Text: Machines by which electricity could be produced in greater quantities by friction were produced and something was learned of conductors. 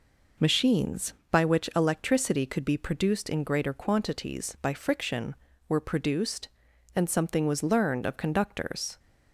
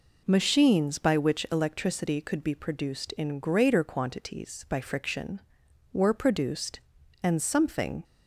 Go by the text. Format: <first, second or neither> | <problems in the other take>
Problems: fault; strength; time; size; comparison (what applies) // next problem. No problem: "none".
first | stops before "was learned of conductors"; at 8.0 s